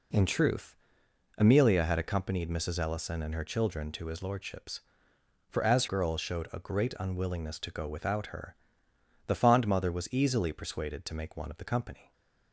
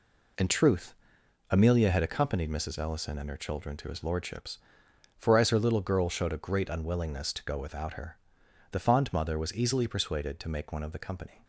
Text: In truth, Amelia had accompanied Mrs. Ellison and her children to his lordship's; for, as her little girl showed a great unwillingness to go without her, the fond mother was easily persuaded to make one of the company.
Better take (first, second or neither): second